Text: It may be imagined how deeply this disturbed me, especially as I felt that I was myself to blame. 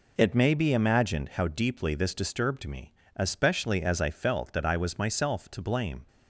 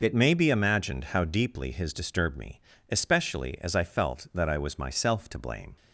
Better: first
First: none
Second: says "his" for "this"; at 1.6 s

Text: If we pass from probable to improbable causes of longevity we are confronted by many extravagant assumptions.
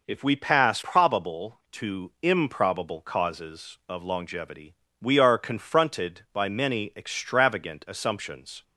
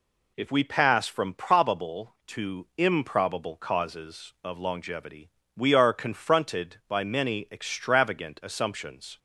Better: second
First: skips "from"; at 0.7 s // pauses between "longevity" and "we"; slight; at 4.7 s; 0.26 s long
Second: pauses between "longevity" and "we"; slight; at 5.2 s; 0.26 s long

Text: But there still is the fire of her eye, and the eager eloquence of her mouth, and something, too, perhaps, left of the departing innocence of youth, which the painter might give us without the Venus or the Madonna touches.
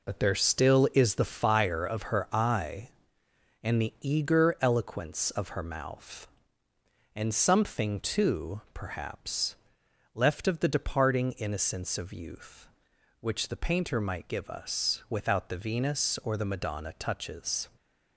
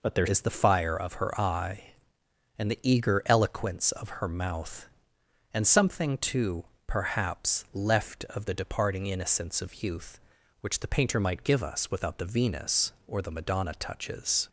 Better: first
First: none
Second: skips "still"; at 0.2 s

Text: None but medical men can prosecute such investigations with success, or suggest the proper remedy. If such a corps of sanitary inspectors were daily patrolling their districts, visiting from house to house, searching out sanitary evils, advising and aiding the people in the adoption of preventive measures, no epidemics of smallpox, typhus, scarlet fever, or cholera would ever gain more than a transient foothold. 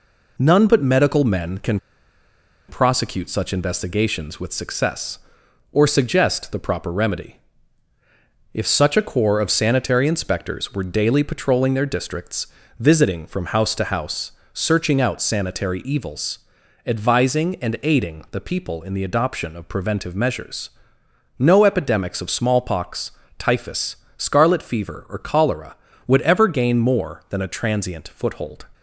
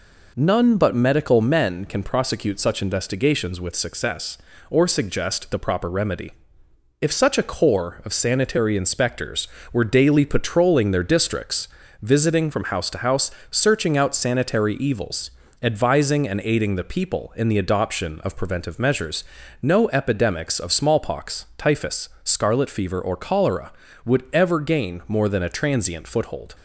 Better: second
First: pauses between "can" and "prosecute"; noticeable; at 1.7 s; 0.89 s long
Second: none

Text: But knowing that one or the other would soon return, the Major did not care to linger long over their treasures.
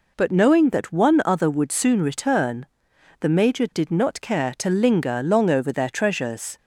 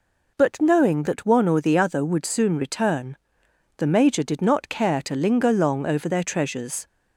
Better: second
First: skips "or the"; at 1.2 s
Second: none

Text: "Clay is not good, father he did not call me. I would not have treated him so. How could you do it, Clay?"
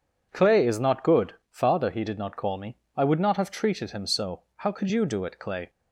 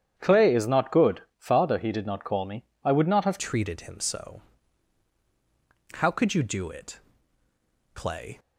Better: first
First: none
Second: starts louder than the rest; strong; until 1.1 s; 9 dB // changes voice at "treated"; from 3.3 s on; 5.0 s long

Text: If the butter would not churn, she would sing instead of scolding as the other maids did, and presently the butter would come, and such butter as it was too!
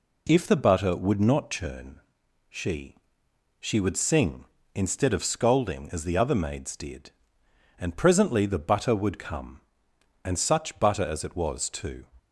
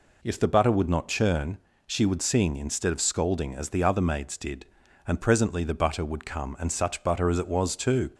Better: second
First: says "she" twice; at 3.6 s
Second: none

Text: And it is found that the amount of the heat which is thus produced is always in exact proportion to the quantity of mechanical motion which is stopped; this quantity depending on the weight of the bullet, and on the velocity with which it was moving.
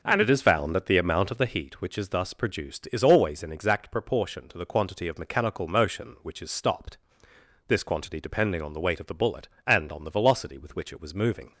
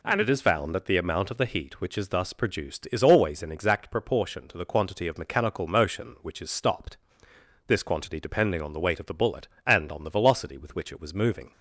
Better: second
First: starts louder than the rest; noticeable; until 1.6 s; 5 dB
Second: none

